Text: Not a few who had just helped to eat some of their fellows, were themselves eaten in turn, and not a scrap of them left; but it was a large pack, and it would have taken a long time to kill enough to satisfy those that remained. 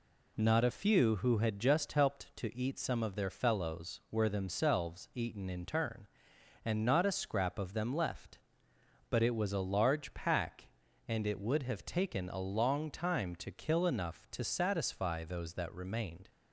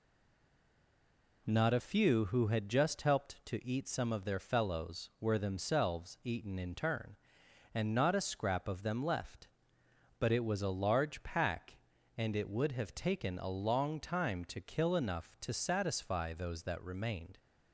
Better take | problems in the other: first | stays silent before the first word; noticeable; until 1.4 s; 1.4 s long

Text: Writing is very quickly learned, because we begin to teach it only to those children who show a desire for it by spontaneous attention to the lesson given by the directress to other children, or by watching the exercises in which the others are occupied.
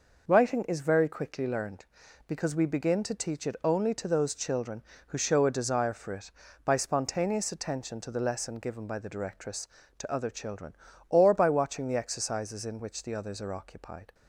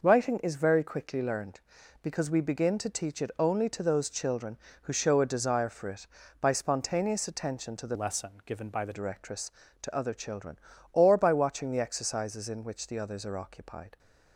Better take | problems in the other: first | changes voice from "lesson" to "the"; from 7.9 to 8.9 s; 1.0 s long // pauses between "lesson" and "given"; slight; at 8.3 s; 0.16 s long

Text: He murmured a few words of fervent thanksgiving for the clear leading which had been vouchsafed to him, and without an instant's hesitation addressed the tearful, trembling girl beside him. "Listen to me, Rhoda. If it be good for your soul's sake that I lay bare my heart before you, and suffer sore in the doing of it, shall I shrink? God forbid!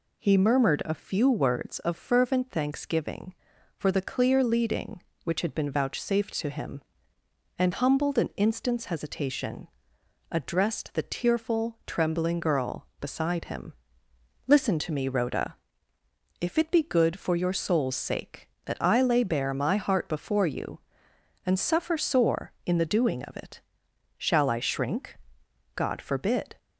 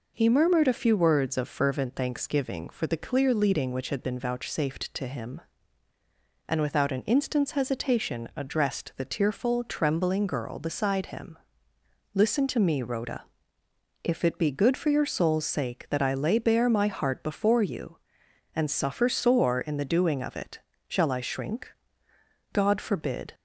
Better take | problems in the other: second | says "humbled" for "without"; at 7.7 s // pauses between "hesitation" and "addressed"; noticeable; at 9.6 s; 0.62 s long

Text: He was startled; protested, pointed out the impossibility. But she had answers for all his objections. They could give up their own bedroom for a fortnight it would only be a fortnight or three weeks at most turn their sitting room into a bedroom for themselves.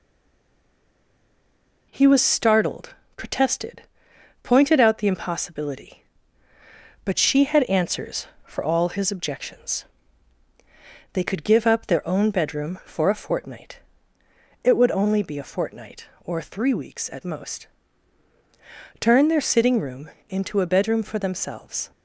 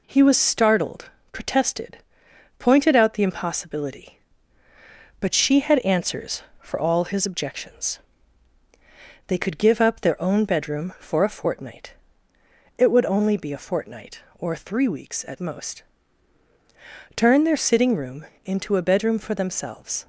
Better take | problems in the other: second | stays silent before the first word; noticeable; until 1.9 s; 1.9 s long // pauses between "fortnight" and "it"; noticeable; at 13.8 s; 0.82 s long; noticeable in the second // pauses between "most" and "turn"; strong; at 17.6 s; 1.3 s long; strong in the second // pauses between "room" and "into"; slight; at 20.1 s; 0.18 s long; slight in the second

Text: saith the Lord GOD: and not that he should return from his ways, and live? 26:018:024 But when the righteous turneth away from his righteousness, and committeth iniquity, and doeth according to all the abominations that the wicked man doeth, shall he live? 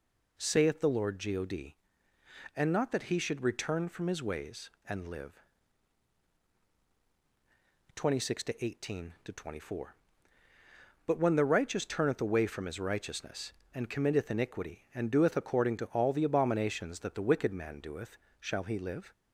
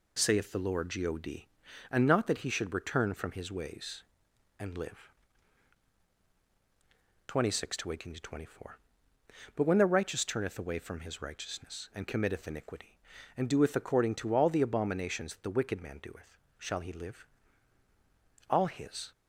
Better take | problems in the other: first | goes on to say "All his"; noticeable; from 18.4 s on; 0.62 s long

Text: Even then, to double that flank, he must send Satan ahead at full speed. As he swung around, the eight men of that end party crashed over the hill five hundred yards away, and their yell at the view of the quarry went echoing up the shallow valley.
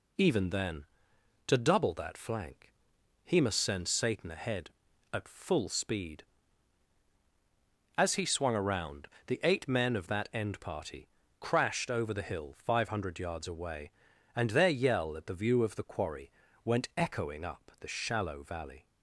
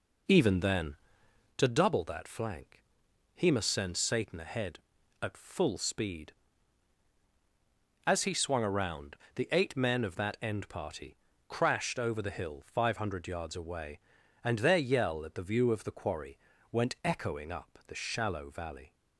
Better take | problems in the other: first | starts louder than the rest; noticeable; until 1.6 s; 4.5 dB // pauses between "party" and "crashed"; slight; at 11.1 s; 0.32 s long; slight in the first // pauses between "quarry" and "went"; slight; at 16.3 s; 0.34 s long; slight in the first

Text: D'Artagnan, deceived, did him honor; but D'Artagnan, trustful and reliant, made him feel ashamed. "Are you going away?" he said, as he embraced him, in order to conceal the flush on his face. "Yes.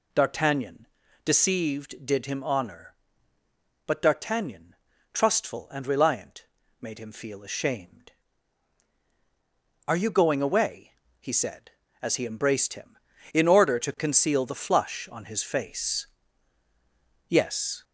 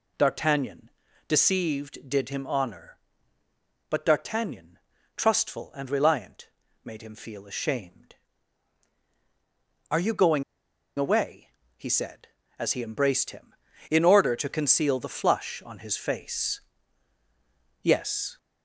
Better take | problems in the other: first | pauses between "going" and "away"; noticeable; at 10.4 s; 0.56 s long

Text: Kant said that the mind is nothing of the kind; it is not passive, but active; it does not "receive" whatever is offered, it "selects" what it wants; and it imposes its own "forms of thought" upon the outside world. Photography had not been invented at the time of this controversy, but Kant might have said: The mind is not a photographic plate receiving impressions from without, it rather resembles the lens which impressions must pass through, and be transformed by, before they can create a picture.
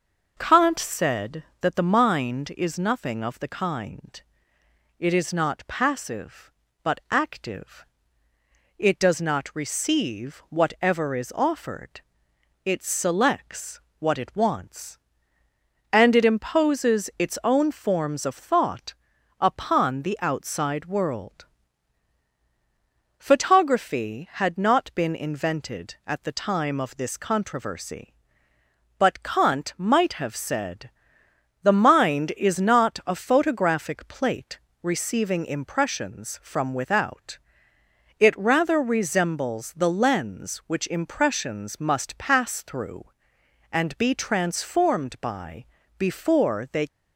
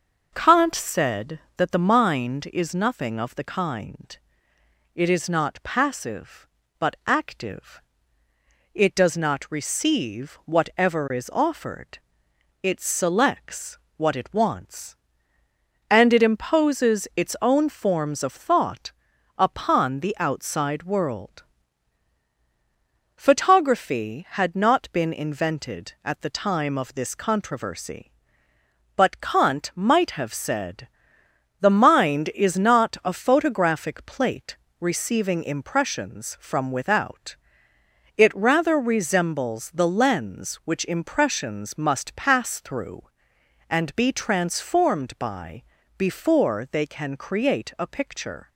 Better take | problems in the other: second | pauses between "selects" and "what"; slight; at 13.7 s; 0.20 s long; slight in the second // pauses between "thought" and "upon"; noticeable; at 18.9 s; 0.46 s long; noticeable in the second // pauses between "plate" and "receiving"; slight; at 34.5 s; 0.24 s long; slight in the second // stops before "can create a picture"; at 46.8 s

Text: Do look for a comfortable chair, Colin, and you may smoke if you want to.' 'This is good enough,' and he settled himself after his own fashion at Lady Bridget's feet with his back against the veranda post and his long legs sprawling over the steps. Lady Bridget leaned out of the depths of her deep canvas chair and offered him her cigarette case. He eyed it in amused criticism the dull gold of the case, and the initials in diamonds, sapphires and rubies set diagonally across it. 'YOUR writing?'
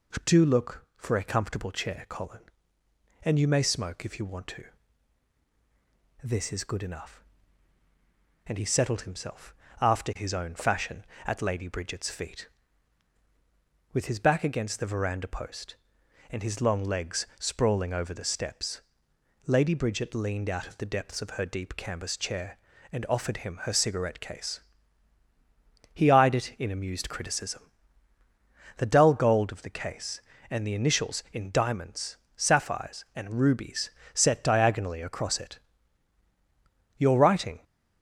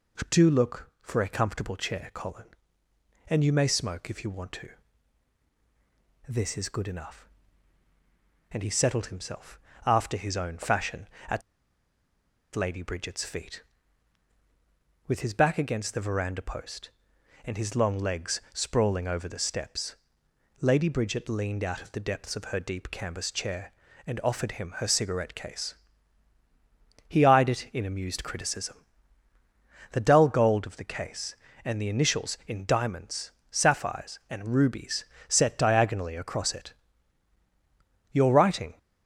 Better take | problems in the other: first | pauses between "himself" and "after"; slight; at 9.5 s; 0.28 s long; slight in the first // pauses between "at" and "Lady"; at 11.4 s; 1.1 s long // pauses between "criticism" and "the"; at 28.8 s; 1.0 s long; also in the first // pauses between "rubies" and "set"; slight; at 35.0 s; 0.24 s long; slight in the first

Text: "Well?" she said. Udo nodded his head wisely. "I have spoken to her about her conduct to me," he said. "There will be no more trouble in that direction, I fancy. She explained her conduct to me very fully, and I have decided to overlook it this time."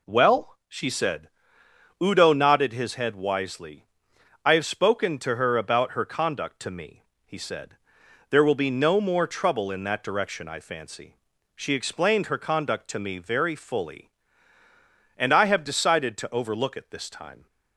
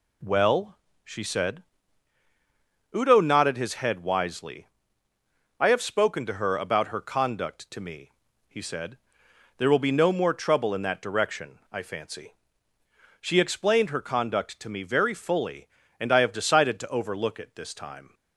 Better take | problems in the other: neither | none

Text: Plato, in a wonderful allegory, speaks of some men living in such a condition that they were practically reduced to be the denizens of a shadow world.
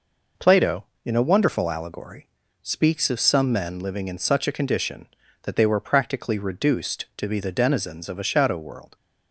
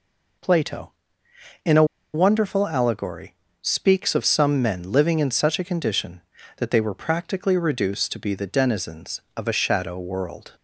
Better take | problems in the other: first | pauses between "a" and "wonderful"; slight; at 1.8 s; 0.29 s long

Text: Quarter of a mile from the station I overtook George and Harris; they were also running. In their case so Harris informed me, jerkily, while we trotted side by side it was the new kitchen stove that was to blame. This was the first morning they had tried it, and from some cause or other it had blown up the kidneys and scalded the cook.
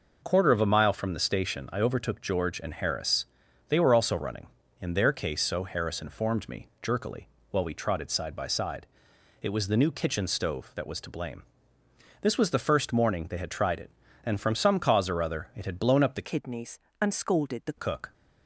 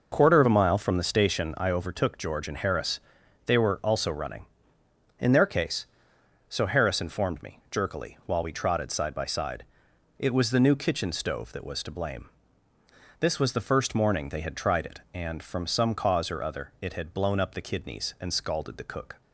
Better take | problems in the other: second | pauses between "side" and "it"; noticeable; at 8.8 s; 0.56 s long; noticeable in the second // changes voice from "kidneys" to "the"; from 16.2 to 17.7 s; 1.5 s long

